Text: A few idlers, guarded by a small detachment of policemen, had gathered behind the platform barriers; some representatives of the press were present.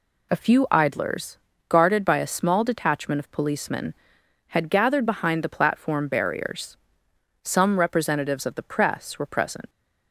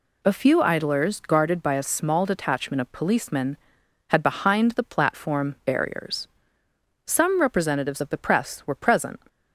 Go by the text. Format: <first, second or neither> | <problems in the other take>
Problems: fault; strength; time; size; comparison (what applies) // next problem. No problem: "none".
first | skips "gathered"; at 4.2 s